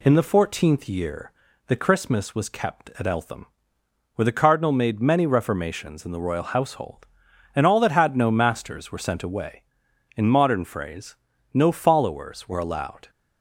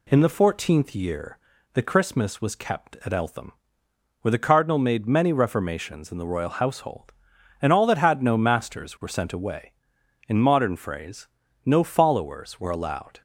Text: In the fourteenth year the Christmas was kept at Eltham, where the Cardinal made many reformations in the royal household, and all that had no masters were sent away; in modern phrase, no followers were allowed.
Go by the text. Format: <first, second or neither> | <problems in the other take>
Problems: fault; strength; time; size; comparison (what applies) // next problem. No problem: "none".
neither | pauses between "year" and "the"; the same in both